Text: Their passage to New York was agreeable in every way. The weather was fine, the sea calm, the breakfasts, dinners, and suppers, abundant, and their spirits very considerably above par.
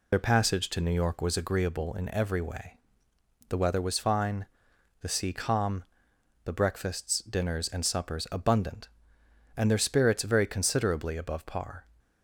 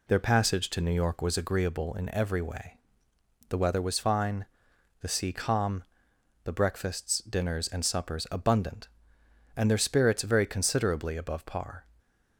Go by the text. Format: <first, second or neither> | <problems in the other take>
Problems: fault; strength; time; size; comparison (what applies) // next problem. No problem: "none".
second | loses the start of "Their"; at 0.1 s; 40 ms